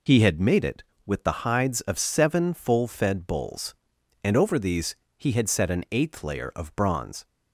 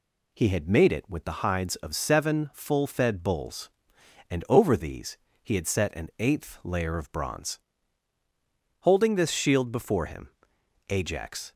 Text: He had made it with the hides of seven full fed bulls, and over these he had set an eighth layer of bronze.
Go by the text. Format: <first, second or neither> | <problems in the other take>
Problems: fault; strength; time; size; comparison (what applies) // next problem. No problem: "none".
first | pauses between "these" and "he"; slight; at 5.1 s; 0.26 s long; slight in the first // goes on to say "Holding this shield before him Ajax"; strong; from 8.8 s on; 2.7 s long